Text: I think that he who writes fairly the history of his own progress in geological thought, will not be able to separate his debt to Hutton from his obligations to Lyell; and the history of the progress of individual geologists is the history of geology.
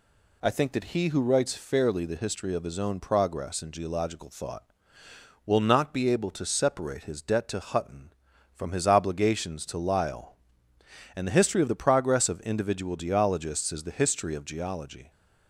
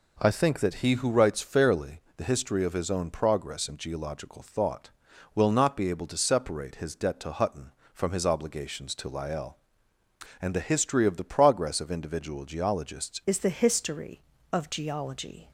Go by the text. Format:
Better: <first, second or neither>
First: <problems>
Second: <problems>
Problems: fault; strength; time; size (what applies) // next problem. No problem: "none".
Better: first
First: none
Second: pauses between "fairly" and "the"; slight; at 1.9 s; 0.18 s long // changes voice at "is"; from 13.2 s on; 2.3 s long